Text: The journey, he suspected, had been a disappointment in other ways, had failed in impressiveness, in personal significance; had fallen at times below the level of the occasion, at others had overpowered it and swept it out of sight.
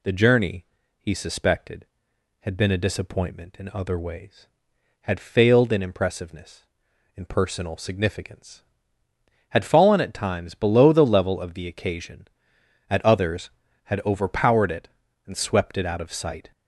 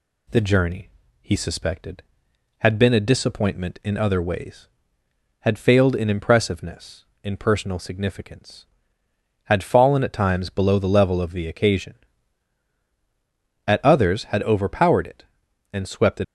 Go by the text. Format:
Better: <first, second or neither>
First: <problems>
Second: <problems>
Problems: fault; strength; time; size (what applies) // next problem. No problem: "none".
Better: first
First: none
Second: stops before "out of sight"; at 16.2 s